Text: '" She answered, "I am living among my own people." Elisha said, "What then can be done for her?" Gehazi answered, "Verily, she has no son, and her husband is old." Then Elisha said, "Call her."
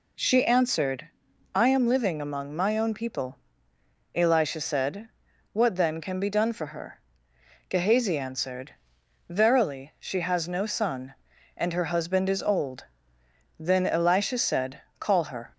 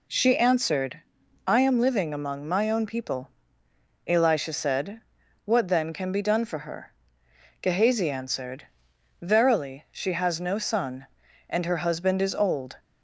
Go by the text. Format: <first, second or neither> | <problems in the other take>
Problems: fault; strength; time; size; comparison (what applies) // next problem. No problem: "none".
first | stops before "Then Elisha said Call her"; at 12.7 s